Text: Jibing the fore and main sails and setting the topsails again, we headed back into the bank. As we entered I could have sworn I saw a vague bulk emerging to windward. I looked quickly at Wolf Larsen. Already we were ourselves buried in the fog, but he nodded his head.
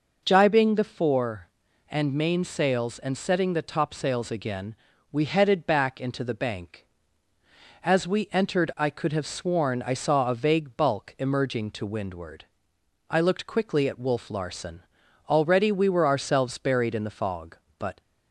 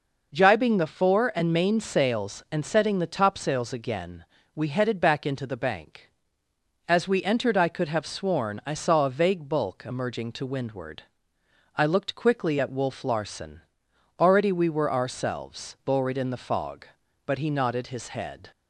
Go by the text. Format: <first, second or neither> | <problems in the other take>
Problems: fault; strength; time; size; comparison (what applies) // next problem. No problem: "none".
second | stops before "he nodded his head"; at 18.0 s